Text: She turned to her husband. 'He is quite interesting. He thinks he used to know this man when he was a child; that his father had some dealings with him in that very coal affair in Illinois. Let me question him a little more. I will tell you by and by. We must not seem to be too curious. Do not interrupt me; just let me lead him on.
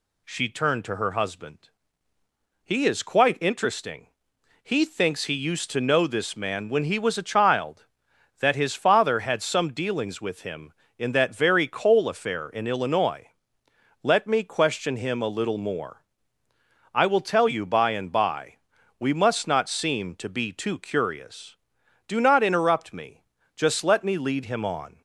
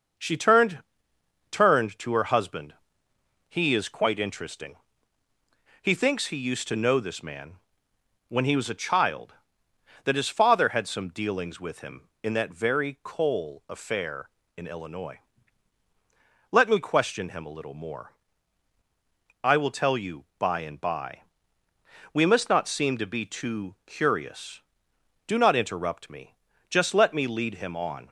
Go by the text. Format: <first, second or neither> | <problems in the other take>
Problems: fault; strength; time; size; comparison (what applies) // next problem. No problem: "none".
first | starts louder than the rest; until 1.8 s; 6 dB // says "turned" twice; at 1.4 s // pauses between "man" and "when"; noticeable; at 7.5 s; 0.70 s long